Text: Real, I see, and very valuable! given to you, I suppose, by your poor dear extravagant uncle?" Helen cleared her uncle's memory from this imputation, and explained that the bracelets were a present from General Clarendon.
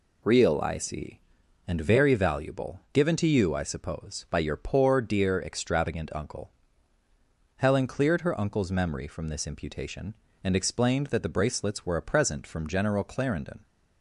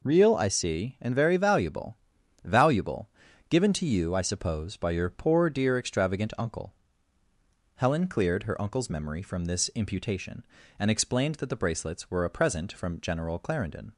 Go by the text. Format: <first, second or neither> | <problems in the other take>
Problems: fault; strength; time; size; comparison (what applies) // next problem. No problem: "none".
first | says "valuable" twice; at 2.4 s